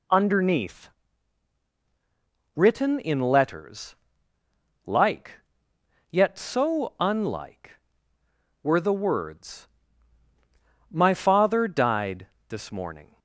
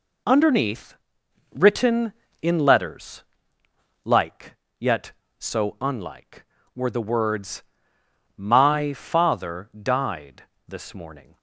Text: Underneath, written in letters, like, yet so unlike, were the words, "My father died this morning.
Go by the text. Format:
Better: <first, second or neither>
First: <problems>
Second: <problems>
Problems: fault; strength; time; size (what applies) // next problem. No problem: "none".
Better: neither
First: pauses between "died" and "this"; slight; at 12.2 s; 0.22 s long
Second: pauses between "died" and "this"; slight; at 10.4 s; 0.24 s long